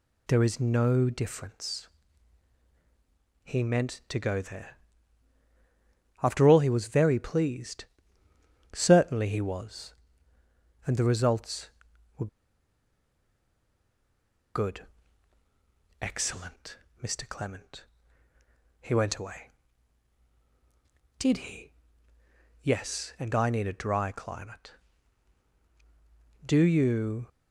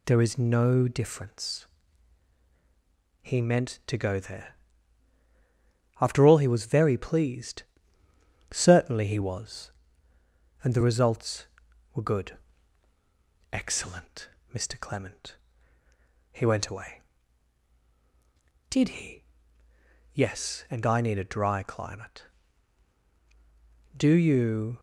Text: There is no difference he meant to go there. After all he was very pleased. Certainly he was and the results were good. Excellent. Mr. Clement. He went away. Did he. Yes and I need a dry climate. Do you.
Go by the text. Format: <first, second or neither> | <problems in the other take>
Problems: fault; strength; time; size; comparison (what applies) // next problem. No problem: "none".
second | pauses between "difference" and "he"; strong; at 1.8 s; 1.5 s long; strong in the second // pauses between "were" and "good"; strong; at 12.2 s; 2.2 s long